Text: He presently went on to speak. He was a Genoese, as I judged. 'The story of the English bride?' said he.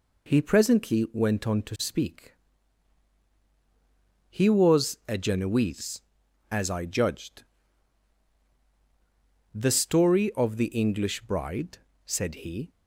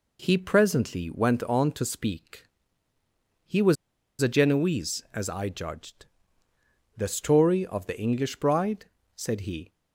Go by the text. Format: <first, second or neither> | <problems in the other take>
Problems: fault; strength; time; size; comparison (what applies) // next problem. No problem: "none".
first | pauses between "was" and "a"; noticeable; at 3.7 s; 0.46 s long